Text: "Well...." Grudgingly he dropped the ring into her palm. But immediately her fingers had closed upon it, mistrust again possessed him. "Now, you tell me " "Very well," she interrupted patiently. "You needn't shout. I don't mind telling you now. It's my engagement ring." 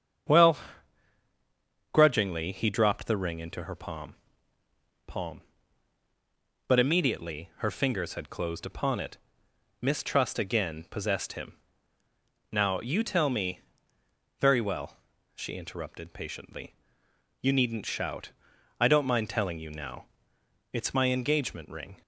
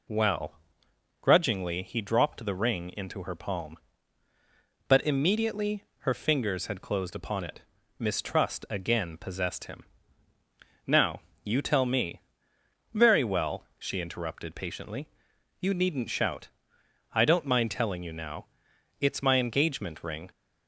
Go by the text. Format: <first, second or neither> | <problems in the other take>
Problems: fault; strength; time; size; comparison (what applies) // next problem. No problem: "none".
second | starts louder than the rest; strong; until 2.6 s; 8 dB // says "palm" twice; at 5.0 s